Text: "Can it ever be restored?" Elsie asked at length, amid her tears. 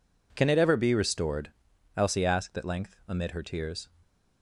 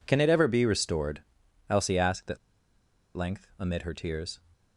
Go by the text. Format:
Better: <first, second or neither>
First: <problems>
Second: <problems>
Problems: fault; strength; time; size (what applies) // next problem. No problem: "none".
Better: first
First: none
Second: pauses between "at" and "length"; noticeable; at 2.3 s; 0.79 s long